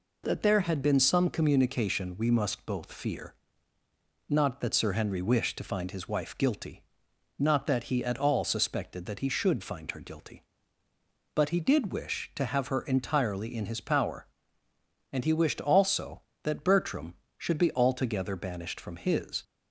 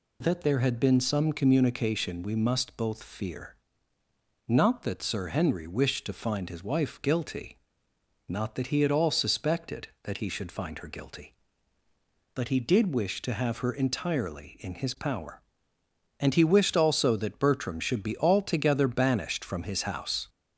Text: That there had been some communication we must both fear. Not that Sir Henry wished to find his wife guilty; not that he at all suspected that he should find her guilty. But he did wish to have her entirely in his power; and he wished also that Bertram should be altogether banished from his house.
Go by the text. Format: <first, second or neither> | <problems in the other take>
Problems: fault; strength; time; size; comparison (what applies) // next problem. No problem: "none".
second | stops before "house"; at 19.4 s